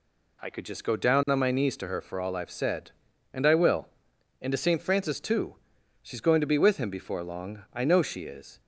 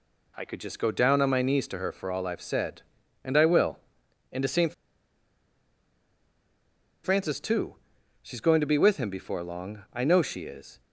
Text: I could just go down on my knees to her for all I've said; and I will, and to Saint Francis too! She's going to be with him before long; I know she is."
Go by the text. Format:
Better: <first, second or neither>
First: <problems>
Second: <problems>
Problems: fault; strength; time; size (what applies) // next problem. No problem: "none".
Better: first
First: none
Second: pauses between "Saint" and "Francis"; strong; at 4.7 s; 2.3 s long